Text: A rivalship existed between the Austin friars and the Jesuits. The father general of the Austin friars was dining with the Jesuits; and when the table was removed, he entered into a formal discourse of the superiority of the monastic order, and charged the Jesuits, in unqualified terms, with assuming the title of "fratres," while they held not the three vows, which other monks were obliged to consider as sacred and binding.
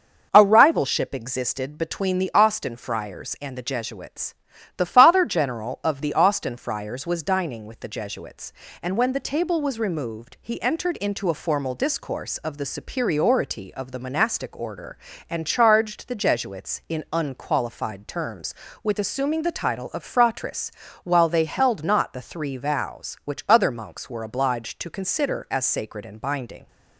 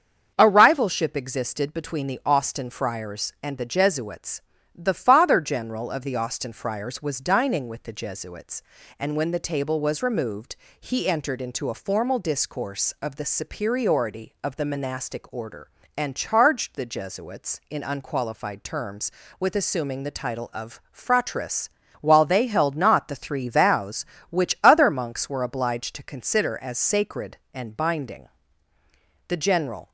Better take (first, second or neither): first